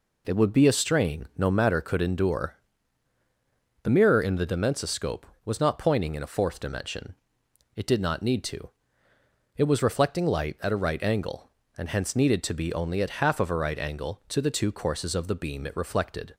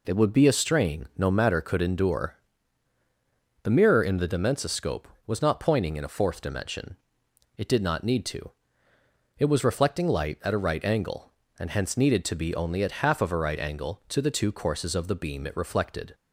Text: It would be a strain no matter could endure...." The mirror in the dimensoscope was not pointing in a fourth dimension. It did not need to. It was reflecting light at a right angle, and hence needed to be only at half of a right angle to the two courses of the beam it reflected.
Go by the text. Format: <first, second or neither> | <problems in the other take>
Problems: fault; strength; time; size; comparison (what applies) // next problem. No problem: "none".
neither | none